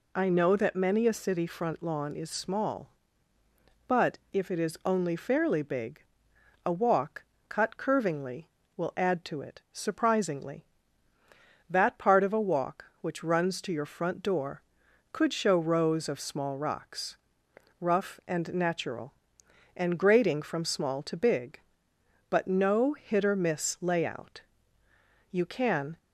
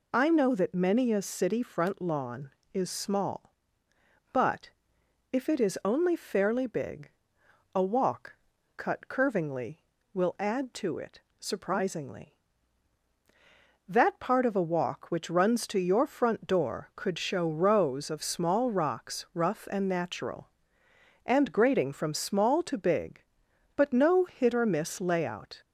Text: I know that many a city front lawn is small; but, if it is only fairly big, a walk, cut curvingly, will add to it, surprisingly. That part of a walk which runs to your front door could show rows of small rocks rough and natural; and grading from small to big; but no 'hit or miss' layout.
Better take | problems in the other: second | pauses between "rocks" and "rough"; noticeable; at 17.1 s; 0.62 s long // goes on to say "You can"; noticeable; from 25.2 s on; 0.68 s long

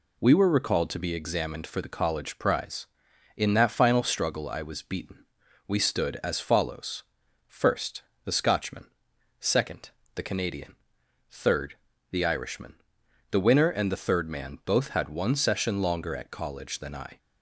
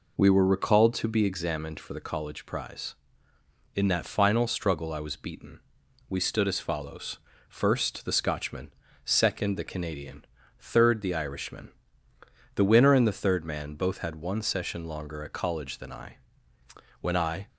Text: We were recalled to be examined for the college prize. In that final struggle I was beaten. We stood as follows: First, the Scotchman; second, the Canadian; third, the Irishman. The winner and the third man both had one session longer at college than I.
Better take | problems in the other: first | goes on to say "When I"; slight; from 17.0 s on; 0.46 s long

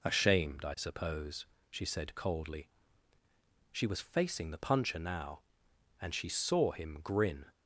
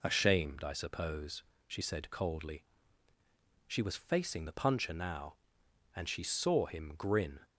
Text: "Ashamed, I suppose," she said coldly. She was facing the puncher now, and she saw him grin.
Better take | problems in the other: neither | none

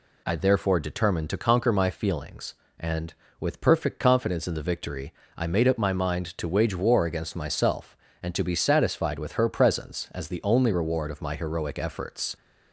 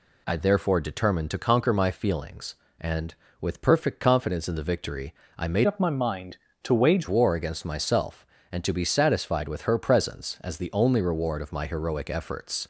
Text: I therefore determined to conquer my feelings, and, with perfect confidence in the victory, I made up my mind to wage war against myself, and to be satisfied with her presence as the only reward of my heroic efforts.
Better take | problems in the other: first | changes voice from "up" to "wage"; from 5.6 to 7.0 s; 1.4 s long

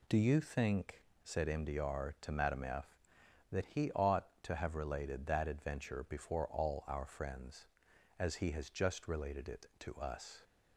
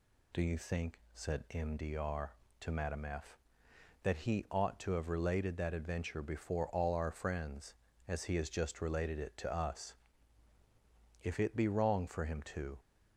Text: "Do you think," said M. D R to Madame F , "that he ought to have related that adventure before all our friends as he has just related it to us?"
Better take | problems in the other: first | goes on to say "If it be wrong for him to"; from 11.2 s on; 1.5 s long

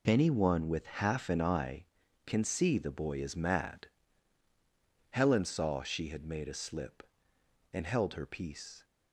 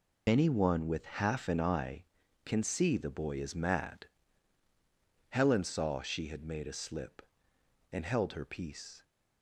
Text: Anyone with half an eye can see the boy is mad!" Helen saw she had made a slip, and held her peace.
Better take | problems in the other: first | loses the start of "Anyone"; at 0.2 s; 30 ms

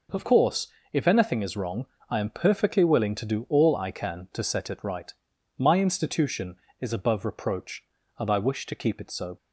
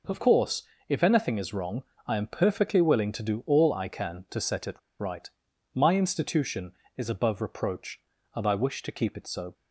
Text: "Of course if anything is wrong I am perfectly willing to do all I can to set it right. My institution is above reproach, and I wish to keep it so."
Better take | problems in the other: first | pauses between "course" and "if"; slight; at 0.6 s; 0.26 s long; slight in the first // pauses between "wrong" and "I"; slight; at 1.8 s; 0.24 s long; slight in the first // pauses between "it" and "right"; slight; at 4.7 s; 0.19 s long

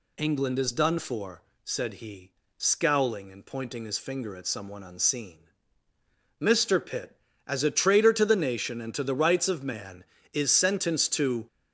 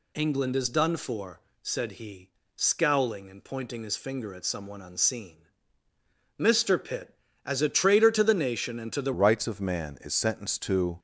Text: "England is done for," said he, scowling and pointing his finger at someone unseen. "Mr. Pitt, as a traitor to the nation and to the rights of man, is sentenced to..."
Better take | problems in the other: first | changes voice at "rights"; from 9.1 s on; 1.8 s long

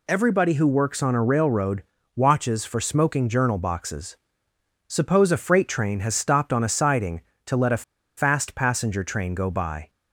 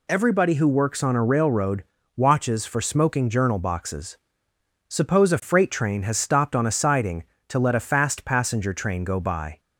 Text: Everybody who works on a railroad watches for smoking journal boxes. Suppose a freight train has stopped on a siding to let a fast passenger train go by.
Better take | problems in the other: second | pauses between "railroad" and "watches"; slight; at 1.8 s; 0.32 s long; slight in the second // pauses between "a" and "fast"; slight; at 7.8 s; 0.34 s long

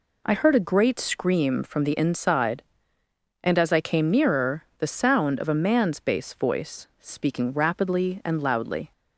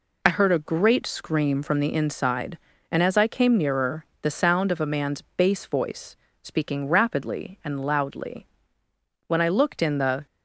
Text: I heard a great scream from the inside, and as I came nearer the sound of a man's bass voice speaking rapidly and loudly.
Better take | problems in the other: first | pauses between "nearer" and "the"; slight; at 4.0 s; 0.16 s long // pauses between "voice" and "speaking"; slight; at 6.1 s; 0.28 s long // goes on to say "When I looked in the"; noticeable; from 9.2 s on; 1.0 s long

